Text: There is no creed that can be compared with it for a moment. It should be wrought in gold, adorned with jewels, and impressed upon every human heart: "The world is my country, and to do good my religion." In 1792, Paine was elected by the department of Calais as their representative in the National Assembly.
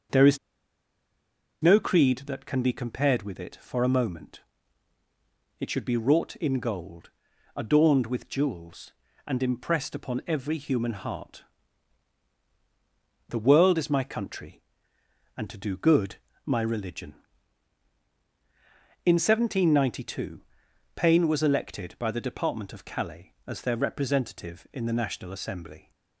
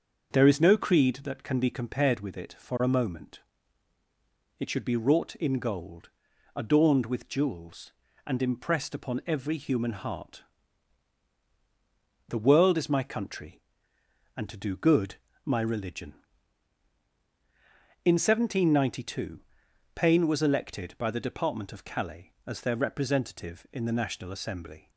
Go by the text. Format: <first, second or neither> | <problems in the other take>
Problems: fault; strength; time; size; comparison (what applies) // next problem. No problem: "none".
second | starts louder than the rest; until 2.4 s; 6.5 dB; also in the second // pauses between "is" and "no"; strong; at 0.3 s; 1.2 s long // pauses between "good" and "my"; slight; at 16.1 s; 0.30 s long; slight in the second